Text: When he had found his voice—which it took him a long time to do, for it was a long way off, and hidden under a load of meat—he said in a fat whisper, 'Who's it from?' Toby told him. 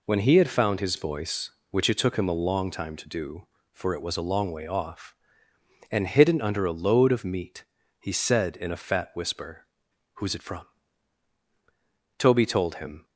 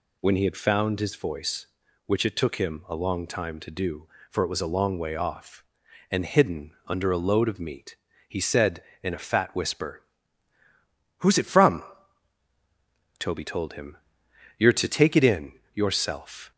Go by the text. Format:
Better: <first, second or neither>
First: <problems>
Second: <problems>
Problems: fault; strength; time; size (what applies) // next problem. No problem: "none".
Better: first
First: none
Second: pauses between "hidden" and "under"; slight; at 6.7 s; 0.16 s long // goes on to say "You're to take it in yourself"; strong; from 14.5 s on; 1.9 s long